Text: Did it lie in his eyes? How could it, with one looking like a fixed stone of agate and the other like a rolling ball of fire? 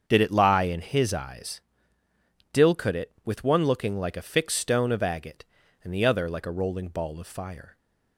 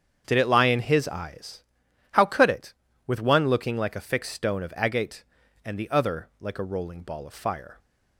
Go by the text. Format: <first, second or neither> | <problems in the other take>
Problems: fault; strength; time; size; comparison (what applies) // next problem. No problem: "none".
second | starts louder than the rest; until 1.0 s; 7 dB; strong in the second // says "Dill" for "How"; at 2.5 s